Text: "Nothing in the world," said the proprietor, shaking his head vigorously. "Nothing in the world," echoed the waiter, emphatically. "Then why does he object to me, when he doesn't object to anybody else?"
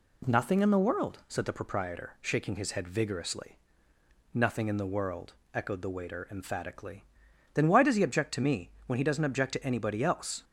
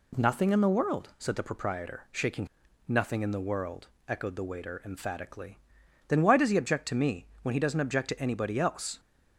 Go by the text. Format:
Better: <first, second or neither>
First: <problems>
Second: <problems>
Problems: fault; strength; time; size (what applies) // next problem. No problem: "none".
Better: first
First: none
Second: skips "his head vigorously"; at 2.6 s